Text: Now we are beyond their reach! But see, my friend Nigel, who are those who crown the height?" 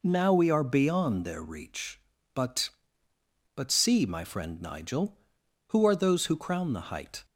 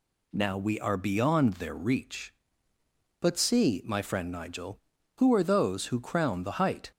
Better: second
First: says "But" twice; at 3.5 s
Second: none

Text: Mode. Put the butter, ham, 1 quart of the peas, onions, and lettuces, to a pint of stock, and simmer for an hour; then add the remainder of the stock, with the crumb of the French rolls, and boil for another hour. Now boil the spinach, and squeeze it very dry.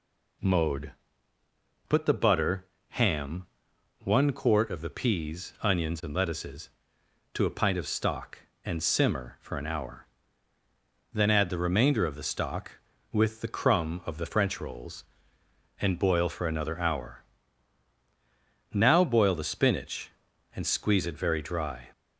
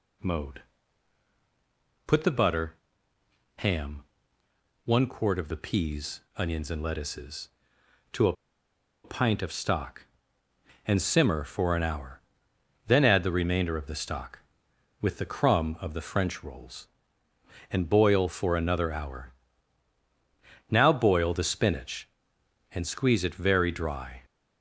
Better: first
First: none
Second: pauses between "a" and "pint"; noticeable; at 8.3 s; 0.71 s long

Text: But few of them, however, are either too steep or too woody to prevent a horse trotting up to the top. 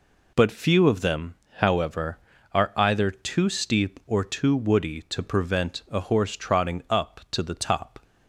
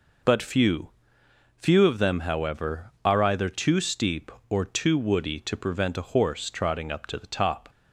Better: first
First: none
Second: says "few" twice; at 1.5 s

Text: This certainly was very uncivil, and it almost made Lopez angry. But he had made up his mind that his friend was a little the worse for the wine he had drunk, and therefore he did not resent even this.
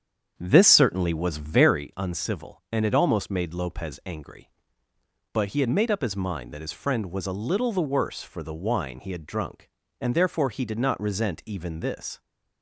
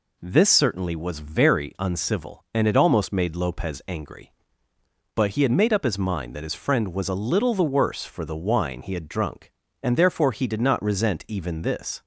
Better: second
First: starts louder than the rest; strong; until 1.9 s; 8 dB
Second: none

